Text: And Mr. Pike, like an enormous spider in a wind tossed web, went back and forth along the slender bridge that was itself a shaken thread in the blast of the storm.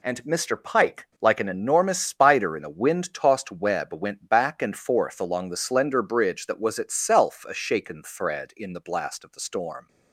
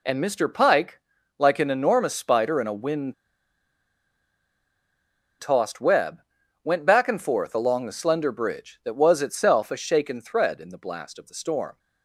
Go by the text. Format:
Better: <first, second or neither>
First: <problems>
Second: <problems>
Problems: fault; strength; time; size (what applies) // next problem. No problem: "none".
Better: first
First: none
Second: pauses between "wind" and "tossed"; strong; at 3.1 s; 2.2 s long